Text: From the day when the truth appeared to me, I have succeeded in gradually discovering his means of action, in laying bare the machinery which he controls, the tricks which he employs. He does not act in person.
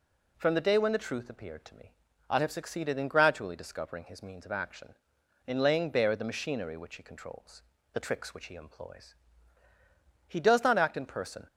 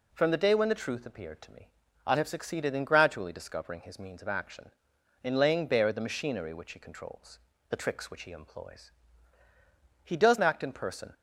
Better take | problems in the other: first | skips "not"; at 10.3 s

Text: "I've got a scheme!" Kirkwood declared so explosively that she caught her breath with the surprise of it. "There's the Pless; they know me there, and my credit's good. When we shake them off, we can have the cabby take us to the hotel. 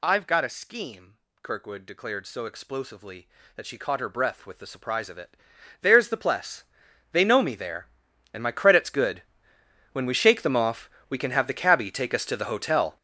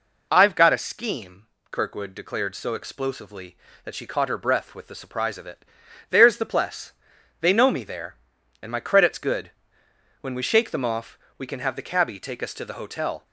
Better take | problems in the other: second | gets louder; strong; throughout; 12.5 dB

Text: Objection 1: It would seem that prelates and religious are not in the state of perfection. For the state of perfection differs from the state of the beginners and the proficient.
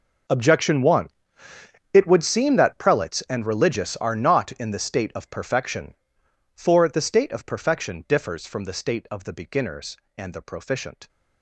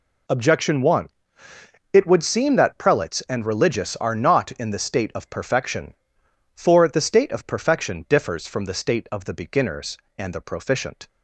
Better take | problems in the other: second | gets quieter; strong; throughout; 18 dB

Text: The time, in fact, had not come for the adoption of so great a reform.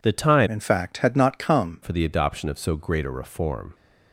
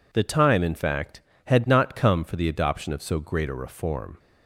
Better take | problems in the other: second | changes voice from "in" to "come"; from 0.4 to 1.8 s; 1.4 s long

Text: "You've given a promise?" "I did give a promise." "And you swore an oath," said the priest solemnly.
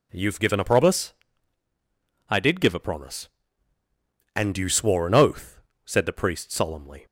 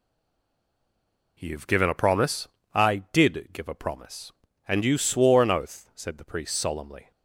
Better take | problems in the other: first | stays silent before the first word; noticeable; until 1.3 s; 1.3 s long

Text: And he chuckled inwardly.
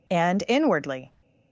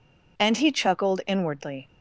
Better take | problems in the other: second | skips "he chuckled"; at 0.4 s

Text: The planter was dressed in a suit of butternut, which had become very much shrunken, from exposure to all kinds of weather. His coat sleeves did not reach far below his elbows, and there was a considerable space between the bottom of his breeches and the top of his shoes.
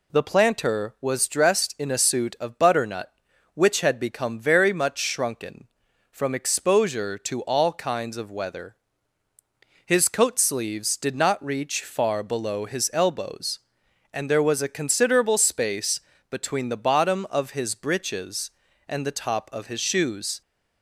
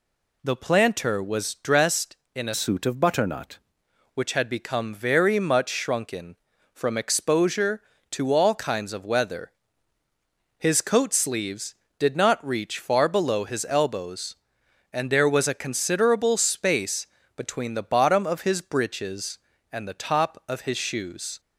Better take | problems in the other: first | changes voice from "suit" to "butternut"; from 2.5 to 3.5 s; 1.0 s long // pauses between "space" and "between"; slight; at 17.0 s; 0.30 s long; slight in the first

